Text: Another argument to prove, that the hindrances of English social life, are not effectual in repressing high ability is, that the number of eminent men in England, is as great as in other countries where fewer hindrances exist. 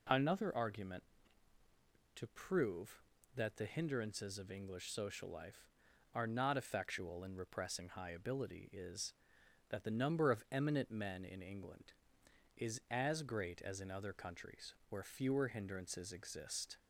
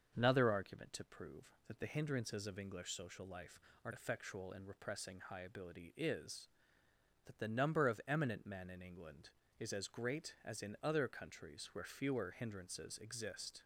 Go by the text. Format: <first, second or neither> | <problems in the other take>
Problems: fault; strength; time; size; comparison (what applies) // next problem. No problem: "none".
first | starts louder than the rest; until 1.1 s; 6.5 dB // skips "not"; at 3.9 s